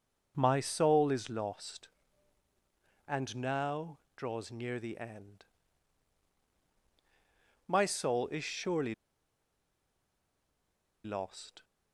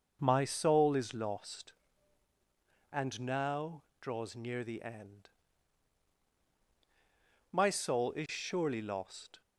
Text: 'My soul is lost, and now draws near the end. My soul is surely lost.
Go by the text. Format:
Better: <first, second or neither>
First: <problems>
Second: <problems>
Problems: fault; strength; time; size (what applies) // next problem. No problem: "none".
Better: second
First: pauses between "now" and "draws"; slight; at 3.9 s; 0.18 s long // pauses between "surely" and "lost"; strong; at 8.9 s; 2.1 s long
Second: pauses between "now" and "draws"; slight; at 3.8 s; 0.18 s long